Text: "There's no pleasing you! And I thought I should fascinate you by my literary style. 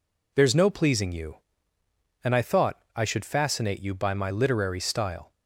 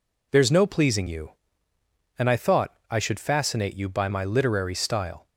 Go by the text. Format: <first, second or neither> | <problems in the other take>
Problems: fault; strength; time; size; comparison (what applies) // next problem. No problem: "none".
neither | none